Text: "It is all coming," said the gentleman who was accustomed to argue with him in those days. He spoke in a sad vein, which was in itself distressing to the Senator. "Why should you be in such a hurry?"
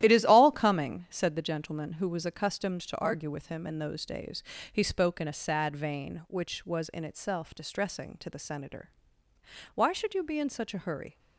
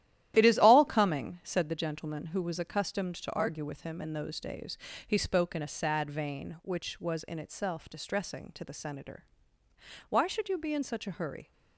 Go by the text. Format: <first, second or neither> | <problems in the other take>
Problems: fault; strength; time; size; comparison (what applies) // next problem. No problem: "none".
neither | starts louder than the rest; strong; the same in both